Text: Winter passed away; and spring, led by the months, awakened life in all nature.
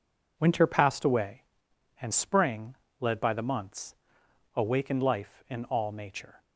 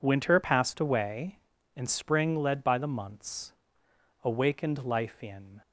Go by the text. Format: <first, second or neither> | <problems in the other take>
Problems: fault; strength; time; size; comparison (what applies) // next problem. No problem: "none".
first | stops before "all nature"; at 5.6 s